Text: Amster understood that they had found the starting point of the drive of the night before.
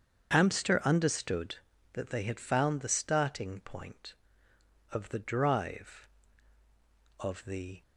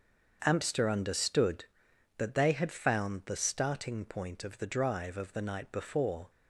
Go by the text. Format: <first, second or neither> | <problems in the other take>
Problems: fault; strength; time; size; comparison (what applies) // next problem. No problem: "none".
second | starts louder than the rest; strong; until 1.3 s; 7 dB; also in the second // stops before "night before"; at 7.8 s